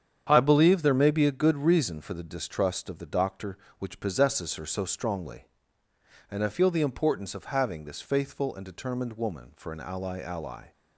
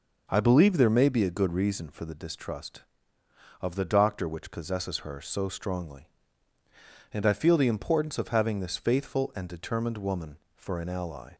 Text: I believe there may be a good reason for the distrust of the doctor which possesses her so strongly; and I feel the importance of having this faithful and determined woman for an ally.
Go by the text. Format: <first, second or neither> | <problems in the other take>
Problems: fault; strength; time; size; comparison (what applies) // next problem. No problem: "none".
second | starts louder than the rest; strong; until 1.3 s; 8.5 dB // says "ally" twice; at 10.1 s